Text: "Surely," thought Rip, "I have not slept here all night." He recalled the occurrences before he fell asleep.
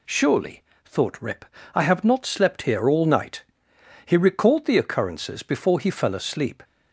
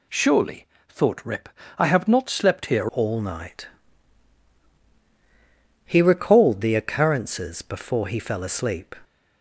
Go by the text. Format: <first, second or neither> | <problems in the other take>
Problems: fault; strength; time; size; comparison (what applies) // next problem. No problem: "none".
first | changes voice at "all"; from 2.9 s on; 6.0 s long